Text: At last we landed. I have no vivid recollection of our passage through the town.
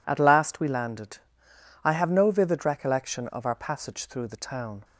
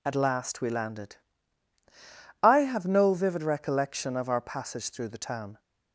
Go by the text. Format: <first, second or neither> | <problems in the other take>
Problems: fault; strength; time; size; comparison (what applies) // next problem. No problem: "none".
neither | none